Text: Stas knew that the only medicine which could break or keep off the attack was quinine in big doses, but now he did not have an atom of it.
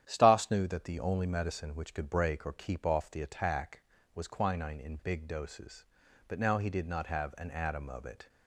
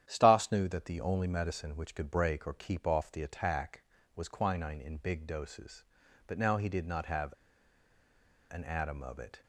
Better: first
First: starts louder than the rest; strong; until 1.0 s; 10 dB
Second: starts louder than the rest; strong; until 1.0 s; 10 dB // pauses between "have" and "an"; at 7.3 s; 1.1 s long

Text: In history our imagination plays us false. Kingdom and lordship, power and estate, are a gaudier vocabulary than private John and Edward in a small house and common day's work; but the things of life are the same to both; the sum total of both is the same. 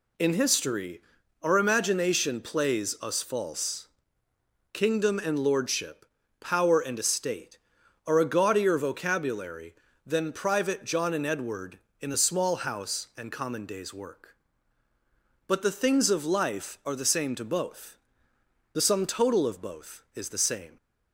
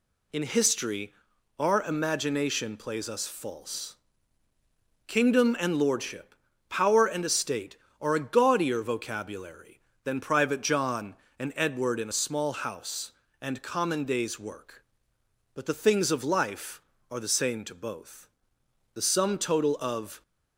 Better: first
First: pauses between "history" and "our"; at 1.0 s; 0.42 s long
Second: pauses between "history" and "our"; at 1.1 s; 0.44 s long // stops before "both is the same"; at 20.2 s

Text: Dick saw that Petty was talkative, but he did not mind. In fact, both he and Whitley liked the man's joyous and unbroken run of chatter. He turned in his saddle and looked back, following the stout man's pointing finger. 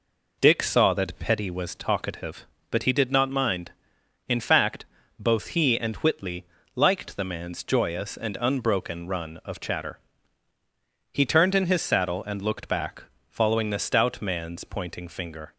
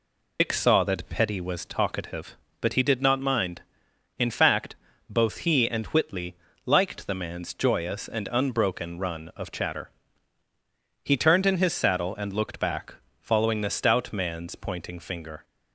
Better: first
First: pauses between "Whitley" and "liked"; slight; at 6.4 s; 0.32 s long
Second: loses the start of "Dick"; at 0.3 s; 95 ms // pauses between "Whitley" and "liked"; slight; at 6.3 s; 0.32 s long

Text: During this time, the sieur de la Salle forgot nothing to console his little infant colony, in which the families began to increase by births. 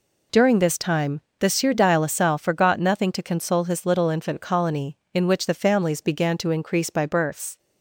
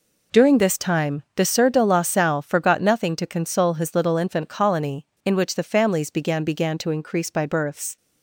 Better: first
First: none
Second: says "began" twice; at 6.4 s

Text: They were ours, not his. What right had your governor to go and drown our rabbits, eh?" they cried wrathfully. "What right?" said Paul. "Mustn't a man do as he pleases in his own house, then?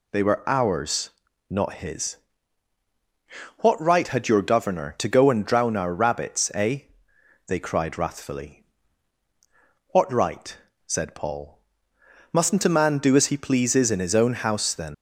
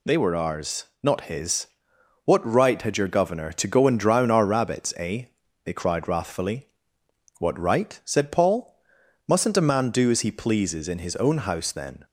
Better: second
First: leaves "then" unfinished; at 14.9 s; 115 ms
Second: none

